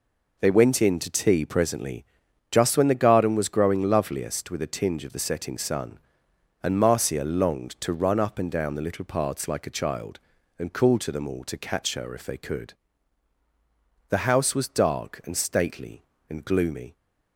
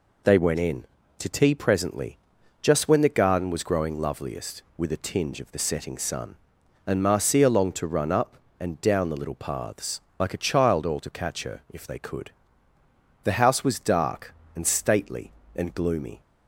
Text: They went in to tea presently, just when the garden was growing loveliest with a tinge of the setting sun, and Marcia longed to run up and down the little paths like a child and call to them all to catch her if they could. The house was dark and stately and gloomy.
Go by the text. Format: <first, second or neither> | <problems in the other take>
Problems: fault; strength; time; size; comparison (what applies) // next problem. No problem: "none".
first | pauses between "paths" and "like"; slight; at 10.0 s; 0.16 s long // skips "and call to them"; at 10.8 s